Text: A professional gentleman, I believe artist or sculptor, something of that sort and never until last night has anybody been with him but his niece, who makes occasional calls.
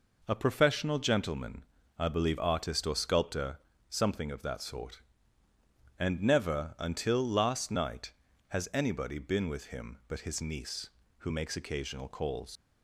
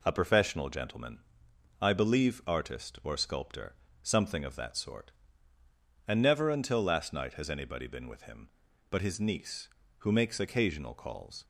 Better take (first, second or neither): second